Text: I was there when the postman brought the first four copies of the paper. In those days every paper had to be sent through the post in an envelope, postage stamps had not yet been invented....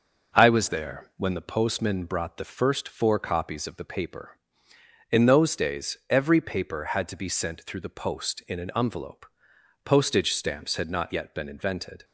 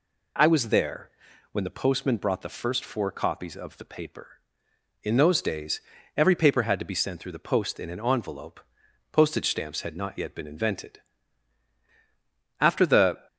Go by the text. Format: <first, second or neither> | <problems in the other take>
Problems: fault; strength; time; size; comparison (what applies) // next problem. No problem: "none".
first | pauses between "there" and "when"; at 1.0 s; 0.42 s long // pauses between "days" and "every"; slight; at 5.8 s; 0.34 s long // goes on to say "After the"; noticeable; from 12.5 s on; 0.68 s long